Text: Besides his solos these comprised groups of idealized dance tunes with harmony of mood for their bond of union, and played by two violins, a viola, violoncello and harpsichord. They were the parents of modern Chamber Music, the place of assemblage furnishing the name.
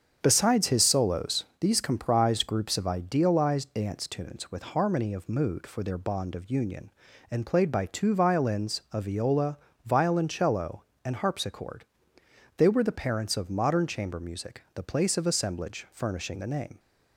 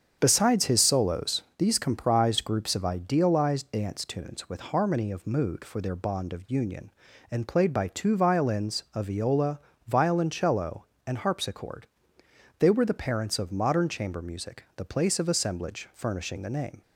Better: neither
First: starts louder than the rest; strong; until 1.2 s; 7.5 dB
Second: starts louder than the rest; strong; until 1.2 s; 7.5 dB

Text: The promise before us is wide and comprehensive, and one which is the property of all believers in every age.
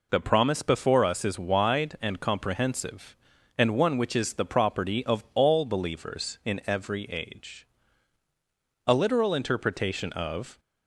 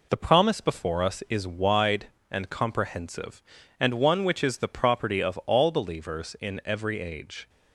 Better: second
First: goes on to say "A literal interpretation of"; strong; from 8.8 s on; 1.7 s long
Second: none

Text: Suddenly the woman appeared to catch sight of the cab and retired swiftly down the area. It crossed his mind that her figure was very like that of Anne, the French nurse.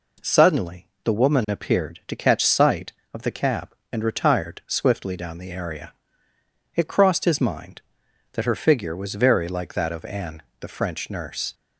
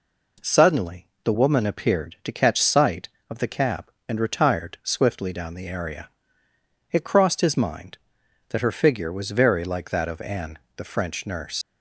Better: first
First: pauses between "Suddenly" and "the"; slight; at 0.8 s; 0.18 s long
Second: pauses between "Suddenly" and "the"; slight; at 1.0 s; 0.18 s long // leaves "nurse" unfinished; at 11.6 s; 85 ms

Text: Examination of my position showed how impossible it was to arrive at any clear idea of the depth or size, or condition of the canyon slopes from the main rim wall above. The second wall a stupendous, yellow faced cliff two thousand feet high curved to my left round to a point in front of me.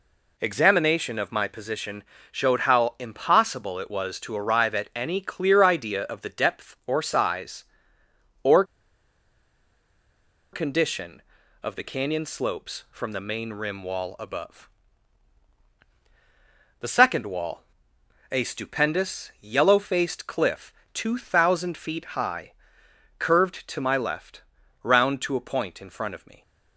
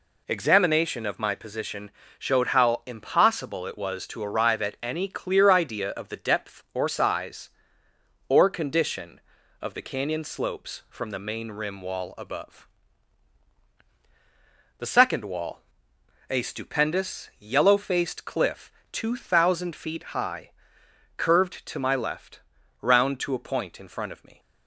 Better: second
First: pauses between "position" and "showed"; slight; at 2.0 s; 0.28 s long // pauses between "or" and "condition"; strong; at 8.6 s; 1.8 s long // pauses between "wall" and "a"; noticeable; at 17.6 s; 0.70 s long // pauses between "cliff" and "two"; slight; at 20.7 s; 0.22 s long // pauses between "high" and "curved"; noticeable; at 22.5 s; 0.66 s long // pauses between "left" and "round"; at 24.4 s; 0.40 s long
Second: pauses between "position" and "showed"; slight; at 1.9 s; 0.28 s long // pauses between "wall" and "a"; noticeable; at 15.6 s; 0.70 s long // pauses between "cliff" and "two"; slight; at 18.7 s; 0.22 s long // pauses between "high" and "curved"; noticeable; at 20.5 s; 0.66 s long // pauses between "left" and "round"; at 22.4 s; 0.40 s long

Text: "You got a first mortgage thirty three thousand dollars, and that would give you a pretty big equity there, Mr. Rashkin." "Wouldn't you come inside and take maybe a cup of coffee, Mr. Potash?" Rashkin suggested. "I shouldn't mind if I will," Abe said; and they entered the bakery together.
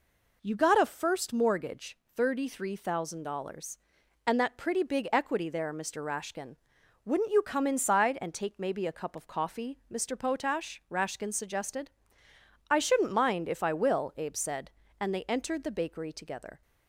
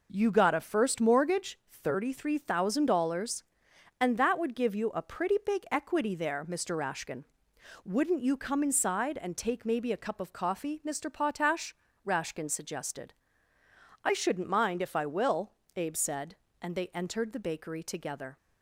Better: second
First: pauses between "mortgage" and "thirty"; slight; at 1.9 s; 0.18 s long // skips "would give you a"; at 4.5 s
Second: none

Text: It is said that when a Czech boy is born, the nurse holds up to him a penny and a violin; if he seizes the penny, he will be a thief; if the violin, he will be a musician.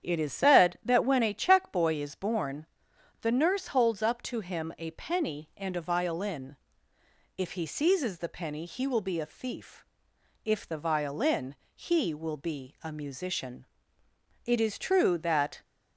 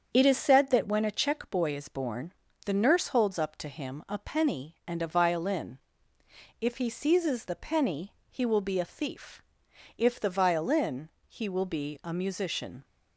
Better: second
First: starts louder than the rest; strong; until 1.1 s; 8.5 dB // goes on to say "It is true that"; noticeable; from 14.4 s on; 1.1 s long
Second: starts louder than the rest; until 1.1 s; 7 dB

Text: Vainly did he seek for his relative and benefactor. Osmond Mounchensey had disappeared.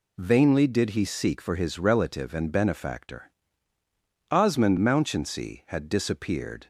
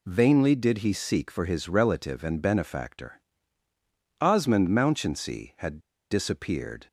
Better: first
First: none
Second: pauses between "had" and "disappeared"; slight; at 5.7 s; 0.31 s long

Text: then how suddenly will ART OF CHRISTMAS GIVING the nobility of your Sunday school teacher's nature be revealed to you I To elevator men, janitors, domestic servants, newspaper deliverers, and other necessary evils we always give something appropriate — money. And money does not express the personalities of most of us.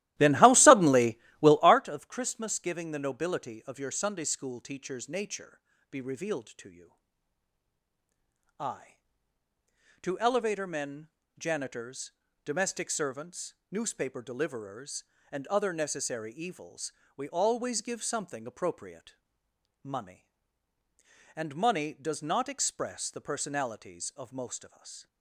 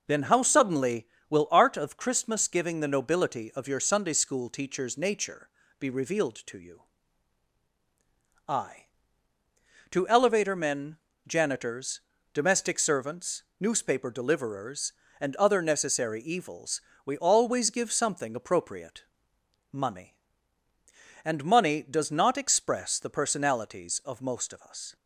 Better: second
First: starts louder than the rest; strong; until 1.8 s; 15.5 dB // pauses between "nature" and "be"; slight; at 5.6 s; 0.30 s long // pauses between "you" and "I"; strong; at 6.9 s; 1.6 s long // pauses between "evils" and "we"; slight; at 16.9 s; 0.24 s long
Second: pauses between "nature" and "be"; slight; at 5.4 s; 0.30 s long // pauses between "you" and "I"; strong; at 6.8 s; 1.6 s long // pauses between "evils" and "we"; slight; at 16.8 s; 0.24 s long

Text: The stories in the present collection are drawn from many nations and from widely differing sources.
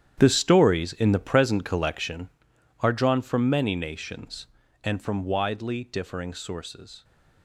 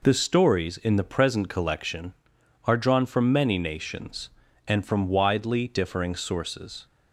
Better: second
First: gets quieter; strong; throughout; 14 dB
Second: none

